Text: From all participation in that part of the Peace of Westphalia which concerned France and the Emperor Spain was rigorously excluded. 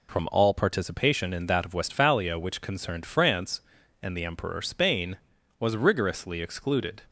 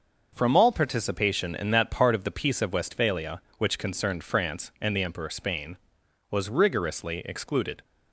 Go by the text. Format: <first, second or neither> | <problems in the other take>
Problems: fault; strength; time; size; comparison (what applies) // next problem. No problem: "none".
second | skips "part of the Peace"; at 1.6 s